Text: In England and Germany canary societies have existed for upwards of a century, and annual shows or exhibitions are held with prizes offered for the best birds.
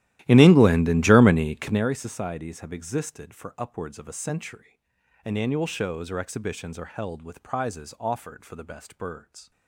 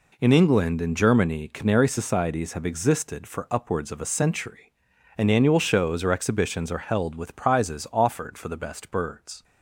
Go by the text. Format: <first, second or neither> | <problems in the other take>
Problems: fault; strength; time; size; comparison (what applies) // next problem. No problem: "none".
second | starts louder than the rest; strong; until 1.9 s; 14.5 dB